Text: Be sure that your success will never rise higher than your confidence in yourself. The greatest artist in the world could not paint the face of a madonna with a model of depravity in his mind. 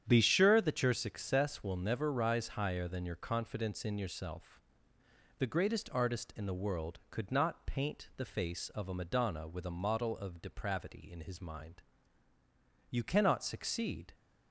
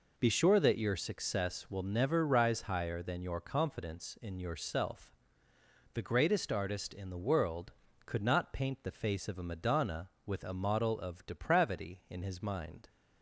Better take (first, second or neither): second